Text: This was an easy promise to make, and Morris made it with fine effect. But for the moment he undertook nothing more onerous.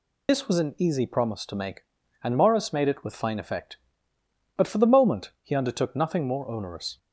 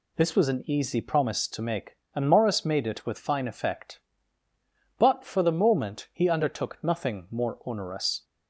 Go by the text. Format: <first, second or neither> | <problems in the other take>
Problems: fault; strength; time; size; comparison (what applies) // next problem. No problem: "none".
second | loses the start of "This"; at 0.2 s; 55 ms